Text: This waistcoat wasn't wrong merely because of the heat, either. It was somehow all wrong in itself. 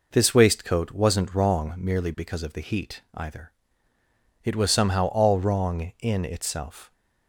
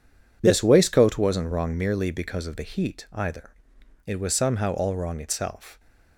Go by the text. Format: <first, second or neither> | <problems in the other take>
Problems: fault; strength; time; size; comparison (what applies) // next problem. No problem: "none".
first | skips "in"; at 5.1 s